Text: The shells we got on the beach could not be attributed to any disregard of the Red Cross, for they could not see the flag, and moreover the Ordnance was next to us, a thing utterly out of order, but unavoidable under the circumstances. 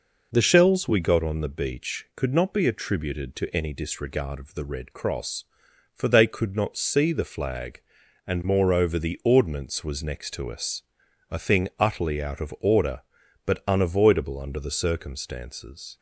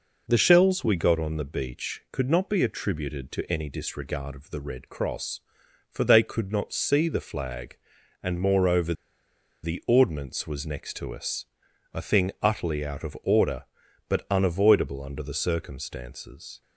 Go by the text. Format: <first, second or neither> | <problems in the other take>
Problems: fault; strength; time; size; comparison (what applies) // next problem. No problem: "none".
first | pauses between "moreover" and "the"; noticeable; at 8.9 s; 0.70 s long